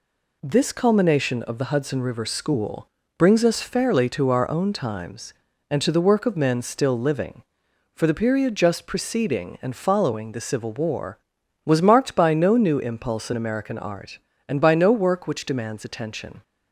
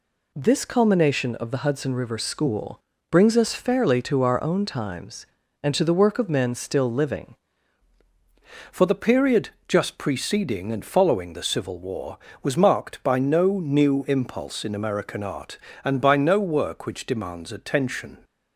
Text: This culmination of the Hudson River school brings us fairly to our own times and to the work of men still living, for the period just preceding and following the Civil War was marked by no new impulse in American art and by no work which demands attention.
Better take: first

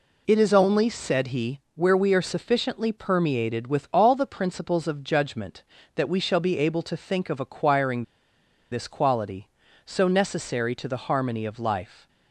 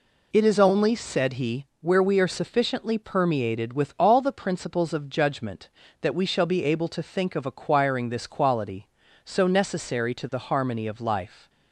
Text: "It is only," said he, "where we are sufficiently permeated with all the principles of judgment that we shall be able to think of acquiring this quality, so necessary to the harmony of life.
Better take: second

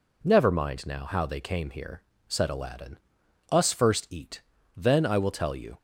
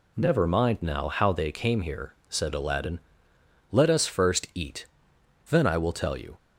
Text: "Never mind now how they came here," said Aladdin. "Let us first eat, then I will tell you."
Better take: second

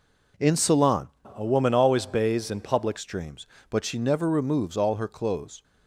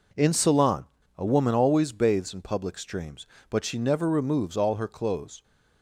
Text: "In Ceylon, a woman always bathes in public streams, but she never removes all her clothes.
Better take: second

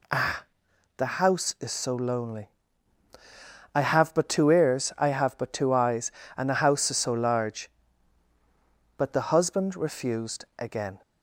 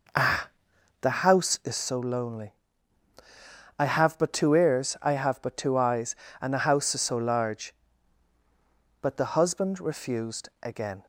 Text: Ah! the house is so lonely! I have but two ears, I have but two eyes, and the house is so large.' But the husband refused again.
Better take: first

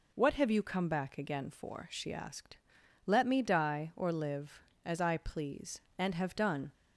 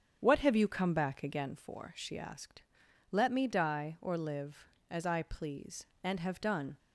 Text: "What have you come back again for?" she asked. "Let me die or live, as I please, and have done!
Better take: first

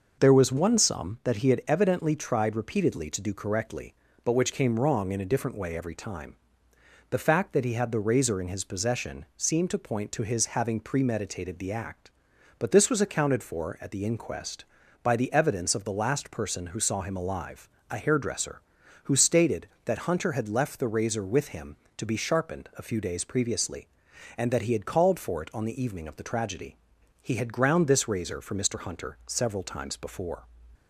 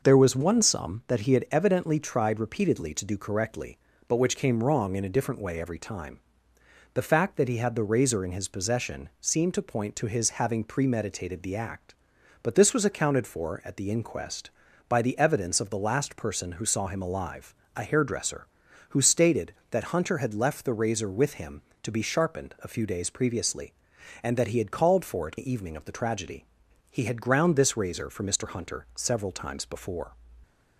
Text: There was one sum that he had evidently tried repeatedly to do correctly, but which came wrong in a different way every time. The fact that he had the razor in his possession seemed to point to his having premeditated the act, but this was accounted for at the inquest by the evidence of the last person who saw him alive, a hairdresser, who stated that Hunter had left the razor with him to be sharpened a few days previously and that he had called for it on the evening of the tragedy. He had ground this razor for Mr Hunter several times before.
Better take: first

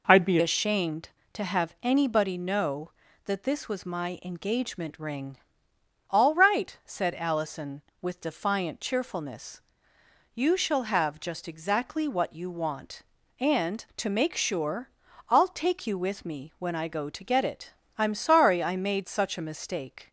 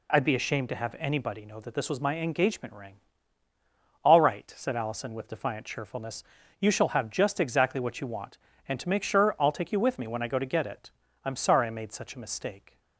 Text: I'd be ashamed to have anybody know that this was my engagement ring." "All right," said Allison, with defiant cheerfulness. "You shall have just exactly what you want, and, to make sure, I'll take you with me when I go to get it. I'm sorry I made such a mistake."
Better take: second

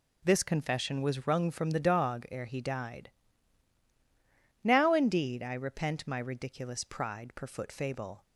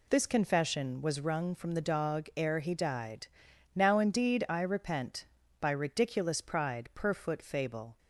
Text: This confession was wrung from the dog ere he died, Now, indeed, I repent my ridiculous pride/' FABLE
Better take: first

